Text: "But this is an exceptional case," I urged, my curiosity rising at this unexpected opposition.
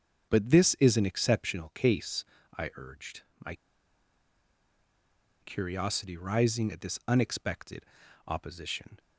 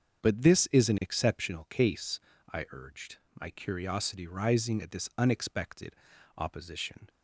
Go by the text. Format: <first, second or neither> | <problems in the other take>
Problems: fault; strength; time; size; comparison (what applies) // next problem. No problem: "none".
second | starts louder than the rest; until 1.3 s; 6.5 dB; also in the second // pauses between "my" and "curiosity"; strong; at 3.5 s; 1.8 s long // pauses between "unexpected" and "opposition"; at 7.8 s; 0.42 s long; also in the second